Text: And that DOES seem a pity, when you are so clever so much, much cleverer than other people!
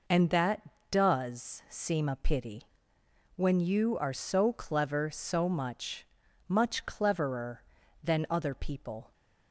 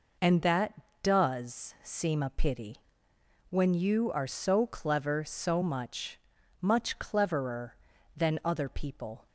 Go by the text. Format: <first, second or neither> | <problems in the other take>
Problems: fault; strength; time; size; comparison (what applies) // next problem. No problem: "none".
neither | none